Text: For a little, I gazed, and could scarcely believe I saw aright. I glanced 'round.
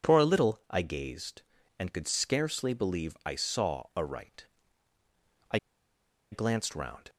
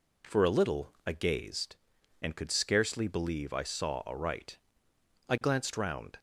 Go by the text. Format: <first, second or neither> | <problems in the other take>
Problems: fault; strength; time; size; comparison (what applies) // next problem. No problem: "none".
second | pauses between "I" and "glanced"; noticeable; at 5.5 s; 0.75 s long